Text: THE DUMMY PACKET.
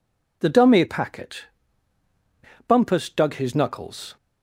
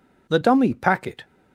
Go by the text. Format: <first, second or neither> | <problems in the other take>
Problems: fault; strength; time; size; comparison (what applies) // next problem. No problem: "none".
second | goes on to say "Bumpus dug his knuckles"; from 2.6 s on; 1.4 s long